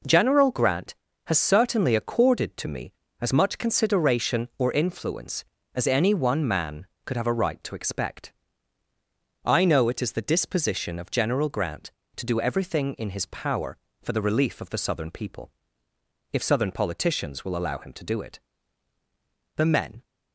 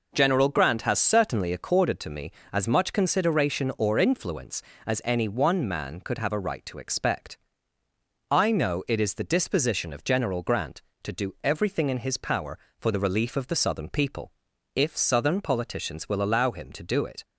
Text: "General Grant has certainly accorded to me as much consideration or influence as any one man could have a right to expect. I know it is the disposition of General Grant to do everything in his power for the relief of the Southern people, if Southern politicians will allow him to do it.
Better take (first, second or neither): second